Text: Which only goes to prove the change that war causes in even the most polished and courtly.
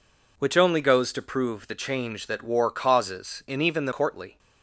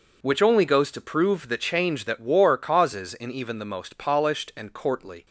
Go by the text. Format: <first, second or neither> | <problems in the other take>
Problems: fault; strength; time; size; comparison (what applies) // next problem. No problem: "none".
second | skips "most polished and"; at 3.9 s